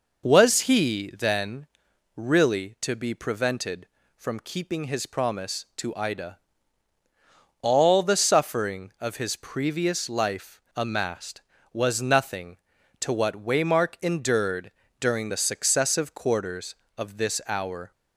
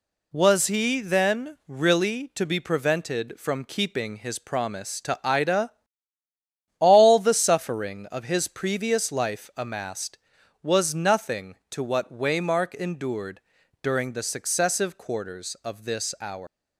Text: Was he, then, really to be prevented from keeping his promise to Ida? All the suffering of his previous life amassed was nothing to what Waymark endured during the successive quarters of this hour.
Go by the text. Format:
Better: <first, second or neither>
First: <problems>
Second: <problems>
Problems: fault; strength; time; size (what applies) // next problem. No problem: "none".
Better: first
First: pauses between "endured" and "during"; slight; at 14.7 s; 0.30 s long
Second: pauses between "endured" and "during"; at 13.3 s; 0.42 s long // leaves "hour" unfinished; at 16.4 s; 145 ms